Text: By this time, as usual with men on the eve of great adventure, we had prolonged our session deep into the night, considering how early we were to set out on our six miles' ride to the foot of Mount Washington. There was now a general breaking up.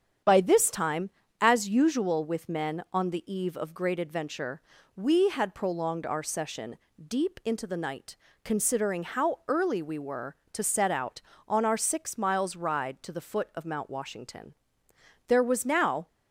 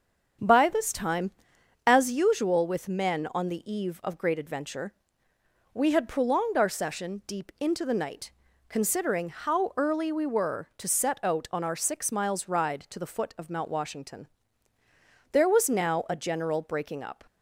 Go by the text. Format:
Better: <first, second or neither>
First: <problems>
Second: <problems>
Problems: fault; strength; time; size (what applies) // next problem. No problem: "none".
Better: second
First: starts louder than the rest; strong; until 1.5 s; 8 dB // pauses between "session" and "deep"; slight; at 6.7 s; 0.28 s long // stops before "a general breaking up"; at 16.0 s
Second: starts louder than the rest; strong; until 1.9 s; 7.5 dB